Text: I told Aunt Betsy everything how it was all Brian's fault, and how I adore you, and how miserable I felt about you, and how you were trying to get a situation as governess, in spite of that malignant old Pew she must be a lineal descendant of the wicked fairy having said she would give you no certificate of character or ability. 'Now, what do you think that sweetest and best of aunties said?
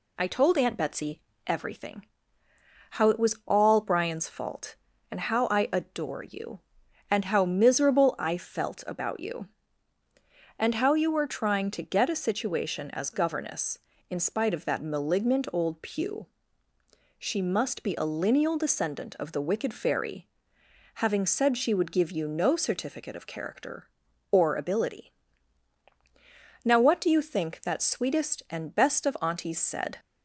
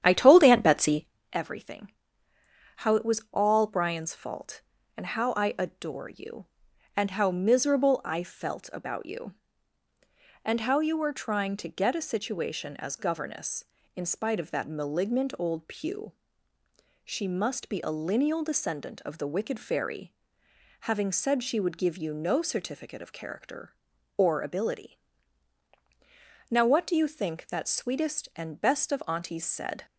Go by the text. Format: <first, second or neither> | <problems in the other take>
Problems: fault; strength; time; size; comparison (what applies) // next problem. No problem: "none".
first | starts louder than the rest; strong; until 1.1 s; 10 dB // pauses between "Betsy" and "everything"; slight; at 1.0 s; 0.26 s long; slight in the first // pauses between "everything" and "how"; noticeable; at 1.9 s; 0.86 s long; noticeable in the first // pauses between "Pew" and "she"; noticeable; at 16.1 s; 0.92 s long; noticeable in the first // pauses between "fairy" and "having"; noticeable; at 20.1 s; 0.68 s long; noticeable in the first